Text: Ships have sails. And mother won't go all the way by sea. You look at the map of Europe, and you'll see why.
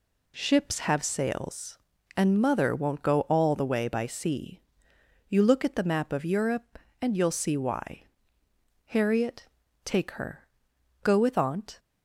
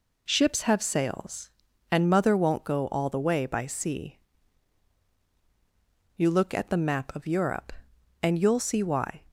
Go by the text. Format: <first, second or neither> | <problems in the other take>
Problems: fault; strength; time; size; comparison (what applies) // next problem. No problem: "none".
second | goes on to say "Harriet take her Go with Aunt"; strong; from 8.8 s on; 2.9 s long